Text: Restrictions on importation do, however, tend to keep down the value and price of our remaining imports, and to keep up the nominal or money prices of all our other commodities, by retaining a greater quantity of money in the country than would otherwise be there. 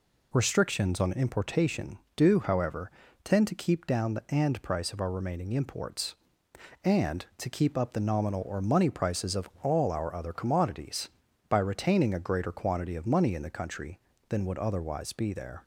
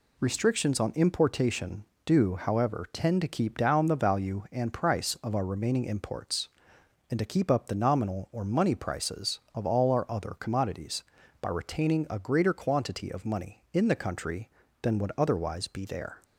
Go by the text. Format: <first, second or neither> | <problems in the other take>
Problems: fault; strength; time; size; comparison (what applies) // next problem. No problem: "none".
second | skips "value"; at 4.2 s